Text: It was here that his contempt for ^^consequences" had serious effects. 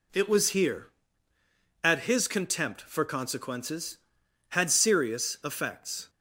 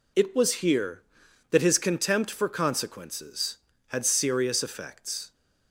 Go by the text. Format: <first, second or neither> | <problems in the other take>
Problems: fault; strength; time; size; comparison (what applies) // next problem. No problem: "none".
second | says "at" for "that"; at 1.8 s